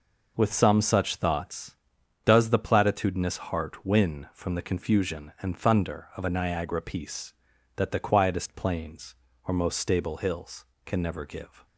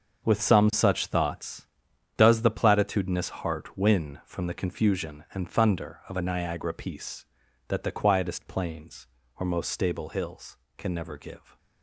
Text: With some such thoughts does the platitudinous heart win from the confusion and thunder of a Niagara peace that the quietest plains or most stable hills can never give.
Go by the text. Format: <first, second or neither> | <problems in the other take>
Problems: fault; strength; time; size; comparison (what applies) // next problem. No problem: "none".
first | gets quieter; strong; throughout; 10.5 dB